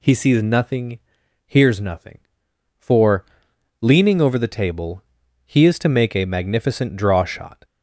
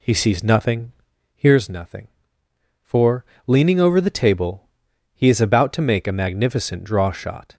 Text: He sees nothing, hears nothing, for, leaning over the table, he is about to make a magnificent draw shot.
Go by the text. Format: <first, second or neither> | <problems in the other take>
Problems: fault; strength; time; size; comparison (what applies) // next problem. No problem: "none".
second | skips "about"; at 5.7 s